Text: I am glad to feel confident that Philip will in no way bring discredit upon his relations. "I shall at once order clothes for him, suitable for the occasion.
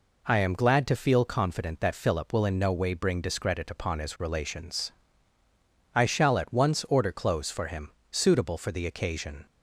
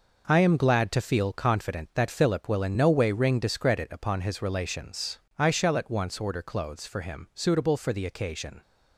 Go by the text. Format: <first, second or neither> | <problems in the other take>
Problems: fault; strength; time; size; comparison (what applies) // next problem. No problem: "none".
first | says "ring" for "bring"; at 3.1 s